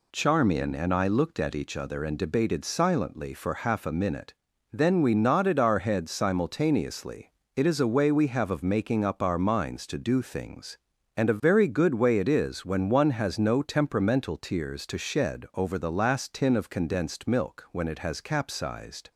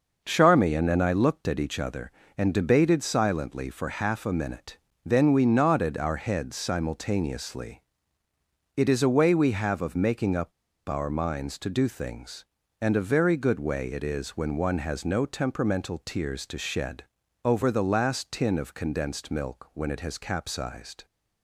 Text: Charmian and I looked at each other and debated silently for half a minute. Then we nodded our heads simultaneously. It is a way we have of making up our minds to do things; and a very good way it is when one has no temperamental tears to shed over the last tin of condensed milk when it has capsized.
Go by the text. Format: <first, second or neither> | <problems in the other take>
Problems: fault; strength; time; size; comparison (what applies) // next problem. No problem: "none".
first | pauses between "up" and "our"; at 10.5 s; 0.37 s long // pauses between "shed" and "over"; at 17.0 s; 0.42 s long